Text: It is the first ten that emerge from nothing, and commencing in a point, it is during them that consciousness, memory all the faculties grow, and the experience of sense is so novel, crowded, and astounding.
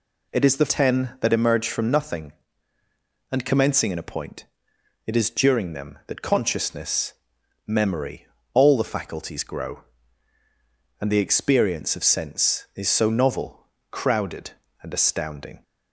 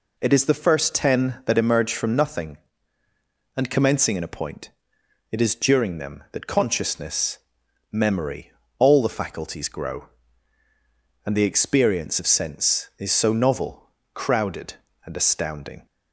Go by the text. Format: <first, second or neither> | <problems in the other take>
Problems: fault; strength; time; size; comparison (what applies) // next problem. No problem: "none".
second | skips "first"; at 0.6 s // pauses between "memory" and "all"; slight; at 8.2 s; 0.28 s long; slight in the second